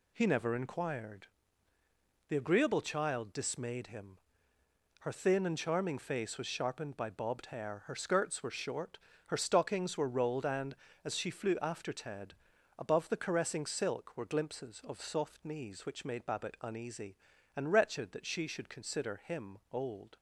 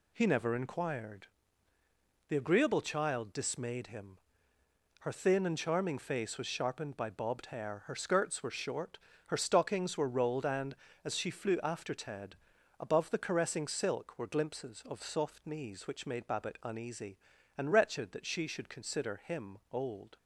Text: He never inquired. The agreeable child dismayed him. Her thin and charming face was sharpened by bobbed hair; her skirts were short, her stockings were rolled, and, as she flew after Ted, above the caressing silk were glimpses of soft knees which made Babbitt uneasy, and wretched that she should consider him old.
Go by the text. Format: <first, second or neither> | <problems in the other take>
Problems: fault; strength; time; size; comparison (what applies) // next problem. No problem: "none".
neither | none